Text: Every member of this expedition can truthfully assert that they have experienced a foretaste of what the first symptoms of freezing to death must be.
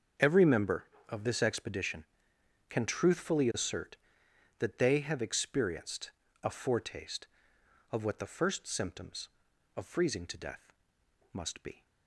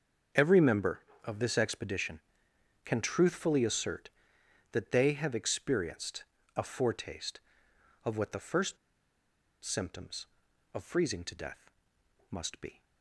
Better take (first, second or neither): first